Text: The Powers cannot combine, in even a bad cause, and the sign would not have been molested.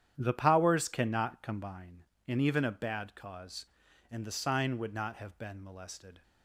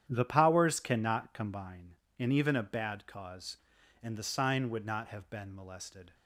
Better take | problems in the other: neither | starts louder than the rest; strong; the same in both

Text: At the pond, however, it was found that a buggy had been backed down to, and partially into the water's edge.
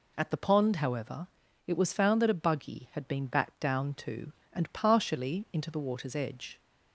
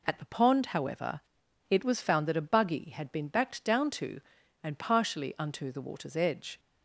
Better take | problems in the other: first | says "unto" for "into"; at 5.3 s

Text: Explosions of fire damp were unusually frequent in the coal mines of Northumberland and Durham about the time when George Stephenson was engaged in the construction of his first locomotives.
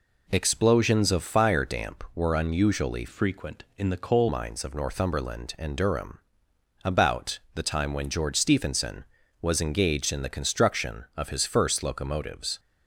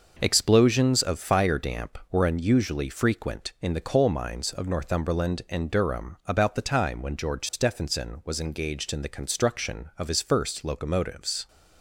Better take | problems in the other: second | changes voice from "frequent" to "coal"; from 3.0 to 4.2 s; 1.2 s long // pauses between "Durham" and "about"; noticeable; at 6.1 s; 0.66 s long // pauses between "about" and "the"; slight; at 7.3 s; 0.16 s long

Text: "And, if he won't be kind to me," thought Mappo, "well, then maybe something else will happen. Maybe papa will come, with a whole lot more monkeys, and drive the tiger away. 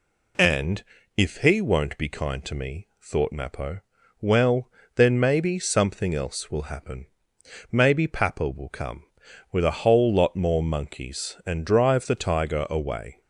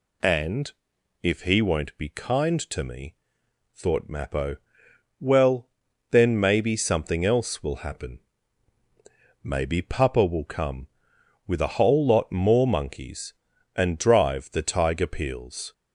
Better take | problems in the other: first | says "peels" for "away"; at 15.0 s

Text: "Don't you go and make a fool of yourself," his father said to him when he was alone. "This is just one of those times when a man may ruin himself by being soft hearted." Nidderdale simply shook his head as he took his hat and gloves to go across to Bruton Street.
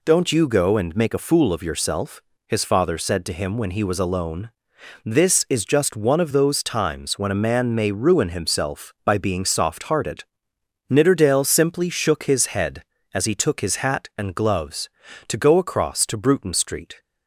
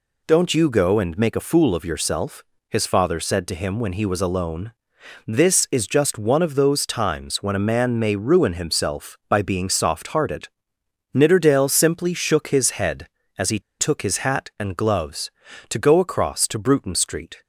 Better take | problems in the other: first | pauses between "he" and "took"; slight; at 13.5 s; 0.20 s long

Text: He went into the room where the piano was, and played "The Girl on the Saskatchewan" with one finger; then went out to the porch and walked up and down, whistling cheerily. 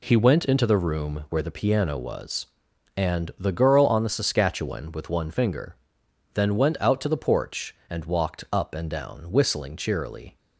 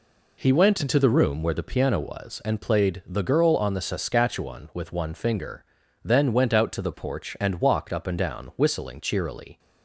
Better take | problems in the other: second | skips "played"; at 3.3 s

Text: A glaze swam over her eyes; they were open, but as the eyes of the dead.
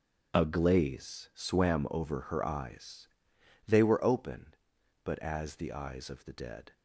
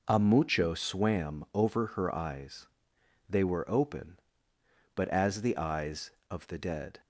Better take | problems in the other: first | says "mucho" for "glaze"; at 0.1 s

